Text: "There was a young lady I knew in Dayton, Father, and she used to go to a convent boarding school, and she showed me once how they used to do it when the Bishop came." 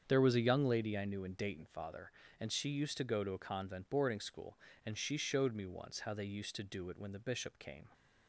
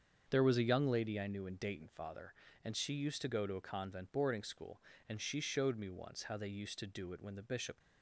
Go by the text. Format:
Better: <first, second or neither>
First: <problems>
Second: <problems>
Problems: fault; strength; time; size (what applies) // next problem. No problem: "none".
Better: first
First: starts louder than the rest; strong; until 1.1 s; 7.5 dB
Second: starts louder than the rest; strong; until 1.3 s; 7 dB // stops before "came"; at 7.8 s